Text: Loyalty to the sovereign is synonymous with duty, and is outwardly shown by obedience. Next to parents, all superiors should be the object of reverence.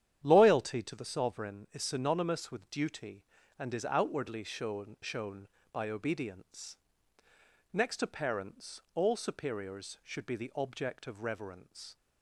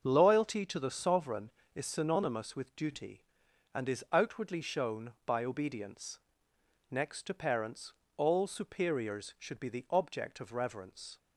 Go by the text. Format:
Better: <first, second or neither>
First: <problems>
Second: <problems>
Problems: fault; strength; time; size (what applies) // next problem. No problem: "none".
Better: second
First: starts louder than the rest; strong; until 1.2 s; 10 dB // says "shown" twice; at 4.9 s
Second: starts louder than the rest; until 1.0 s; 6 dB